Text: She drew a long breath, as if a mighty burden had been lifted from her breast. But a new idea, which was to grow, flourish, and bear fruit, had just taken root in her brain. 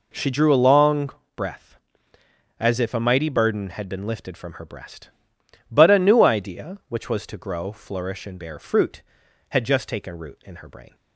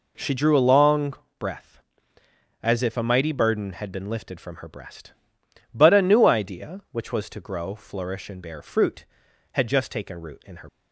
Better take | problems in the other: first | pauses between "long" and "breath"; slight; at 1.1 s; 0.27 s long; slight in the first // stops before "brain"; at 10.6 s

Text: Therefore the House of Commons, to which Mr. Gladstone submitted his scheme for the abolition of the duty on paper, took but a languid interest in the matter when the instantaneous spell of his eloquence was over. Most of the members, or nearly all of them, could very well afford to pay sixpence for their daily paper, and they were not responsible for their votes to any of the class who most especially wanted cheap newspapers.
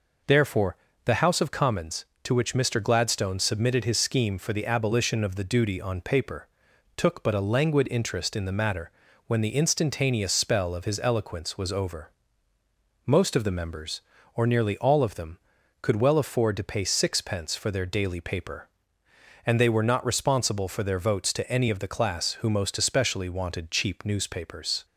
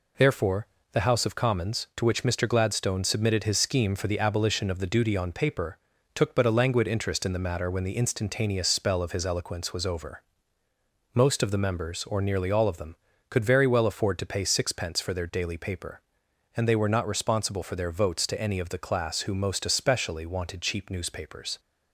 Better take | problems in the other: second | pauses between "Therefore" and "the"; slight; at 0.7 s; 0.28 s long; slight in the second // pauses between "matter" and "when"; at 8.8 s; 0.38 s long // skips "very"; at 15.9 s

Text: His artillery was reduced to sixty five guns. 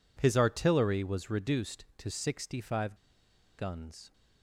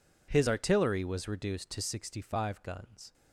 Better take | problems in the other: second | pauses between "five" and "guns"; noticeable; at 2.9 s; 0.62 s long

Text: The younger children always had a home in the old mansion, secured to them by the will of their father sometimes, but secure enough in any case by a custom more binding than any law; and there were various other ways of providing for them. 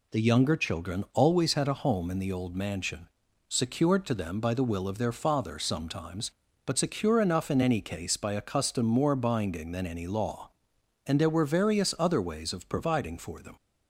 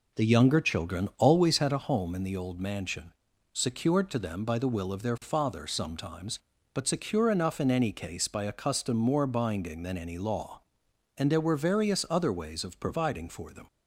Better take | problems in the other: first | starts louder than the rest; until 1.8 s; 4 dB

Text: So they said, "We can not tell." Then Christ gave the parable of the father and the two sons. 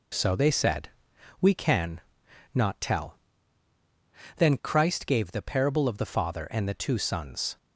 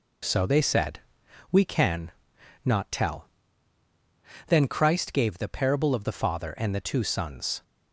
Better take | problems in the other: neither | pauses between "can" and "not"; noticeable; the same in both

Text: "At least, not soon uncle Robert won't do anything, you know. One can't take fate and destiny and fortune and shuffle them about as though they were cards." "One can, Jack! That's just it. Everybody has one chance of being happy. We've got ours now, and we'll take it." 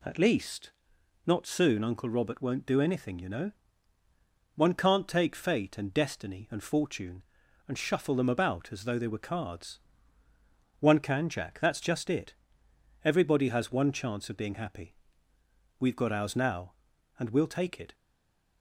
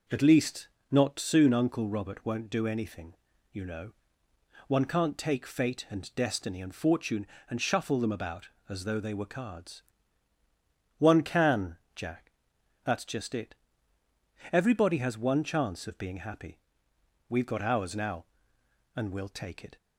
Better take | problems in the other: second | stays silent after the last word; slight; from 17.9 s on; 0.7 s long

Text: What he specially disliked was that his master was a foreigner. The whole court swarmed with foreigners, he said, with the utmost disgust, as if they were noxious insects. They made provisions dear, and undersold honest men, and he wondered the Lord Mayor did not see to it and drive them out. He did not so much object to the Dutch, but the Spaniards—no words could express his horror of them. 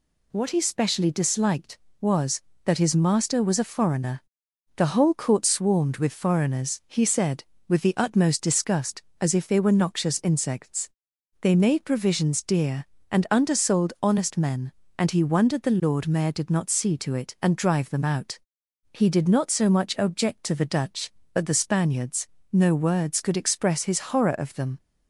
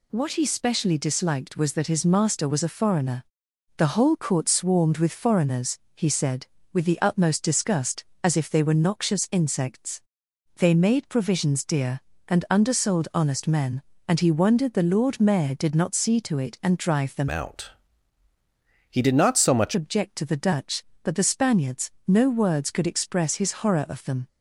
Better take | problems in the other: first | changes voice from "out" to "much"; from 17.2 to 19.7 s; 2.5 s long

